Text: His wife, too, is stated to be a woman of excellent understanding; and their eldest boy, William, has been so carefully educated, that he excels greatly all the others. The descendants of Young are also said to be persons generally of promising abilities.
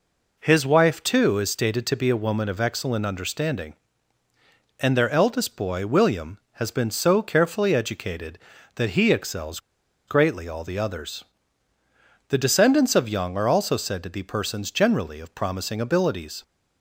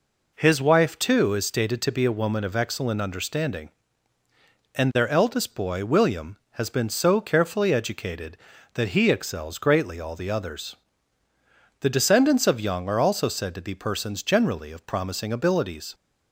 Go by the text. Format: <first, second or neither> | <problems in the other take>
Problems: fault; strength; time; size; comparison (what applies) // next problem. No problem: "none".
second | pauses between "excels" and "greatly"; noticeable; at 9.5 s; 0.49 s long